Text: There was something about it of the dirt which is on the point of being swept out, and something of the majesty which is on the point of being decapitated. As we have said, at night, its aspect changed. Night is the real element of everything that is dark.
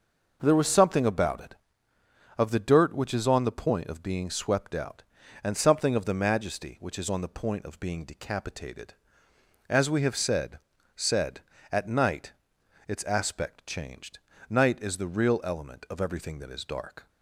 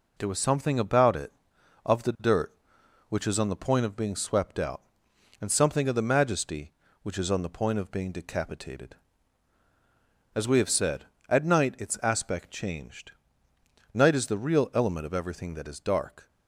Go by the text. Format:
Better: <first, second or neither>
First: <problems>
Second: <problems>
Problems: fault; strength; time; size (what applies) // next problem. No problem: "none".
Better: second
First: says "said" twice; at 10.9 s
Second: none